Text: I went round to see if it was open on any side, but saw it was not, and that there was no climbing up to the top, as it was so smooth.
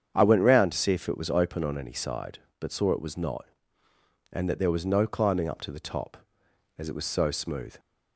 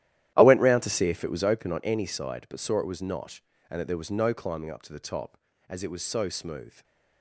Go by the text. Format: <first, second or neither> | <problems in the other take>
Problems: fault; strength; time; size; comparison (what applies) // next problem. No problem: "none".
first | gets quieter; strong; throughout; 15 dB // starts louder than the rest; strong; until 1.3 s; 12.5 dB; strong in the first // stays silent after the last word; slight; from 6.6 s on; 0.6 s long